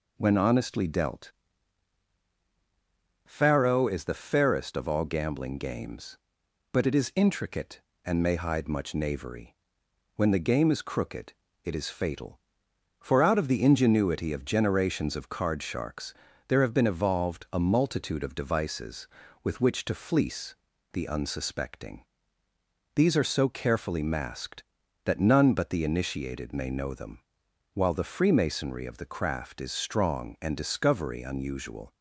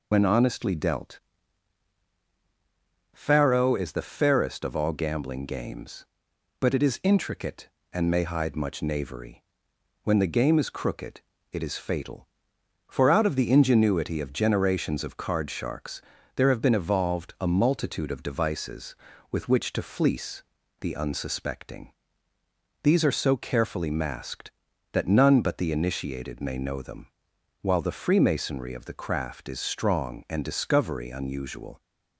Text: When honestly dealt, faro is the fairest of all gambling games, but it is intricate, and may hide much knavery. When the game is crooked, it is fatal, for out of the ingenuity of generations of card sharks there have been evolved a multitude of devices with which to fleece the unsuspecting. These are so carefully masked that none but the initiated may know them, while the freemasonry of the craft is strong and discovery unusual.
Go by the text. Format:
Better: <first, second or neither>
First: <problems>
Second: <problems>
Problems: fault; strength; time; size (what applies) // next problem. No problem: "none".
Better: first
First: pauses between "sharks" and "there"; slight; at 16.1 s; 0.32 s long // pauses between "fleece" and "the"; at 20.5 s; 0.38 s long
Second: loses the start of "When"; at 0.1 s; 55 ms // pauses between "sharks" and "there"; slight; at 16.0 s; 0.32 s long // pauses between "fleece" and "the"; at 20.4 s; 0.38 s long